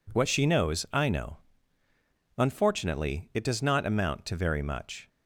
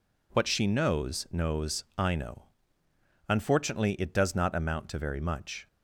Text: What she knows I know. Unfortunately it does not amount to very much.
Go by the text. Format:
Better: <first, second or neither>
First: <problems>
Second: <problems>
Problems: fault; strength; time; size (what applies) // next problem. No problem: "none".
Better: first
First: none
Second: says "knows" twice; at 1.2 s